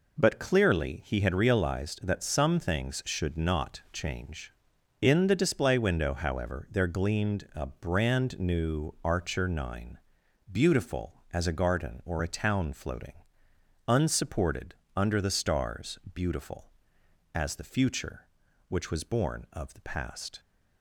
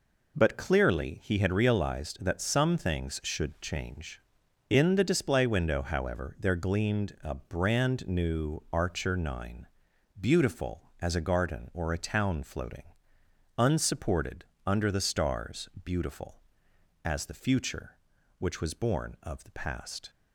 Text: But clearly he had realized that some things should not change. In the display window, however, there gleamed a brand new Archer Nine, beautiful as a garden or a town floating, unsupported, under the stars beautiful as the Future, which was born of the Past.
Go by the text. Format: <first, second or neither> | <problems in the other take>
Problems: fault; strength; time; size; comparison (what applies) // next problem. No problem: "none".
first | skips "not"; at 3.5 s // pauses between "stars" and "beautiful"; slight; at 15.6 s; 0.16 s long; slight in the first